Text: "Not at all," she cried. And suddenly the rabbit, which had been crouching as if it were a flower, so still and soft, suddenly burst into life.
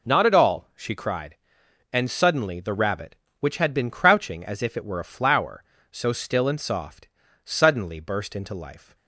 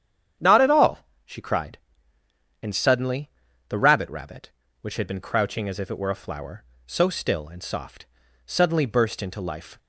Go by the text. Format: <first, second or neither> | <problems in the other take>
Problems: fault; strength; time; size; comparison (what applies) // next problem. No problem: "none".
first | starts louder than the rest; strong; until 1.6 s; 9 dB // pauses between "suddenly" and "the"; at 3.2 s; 0.38 s long // says "rabbit" twice; at 4.0 s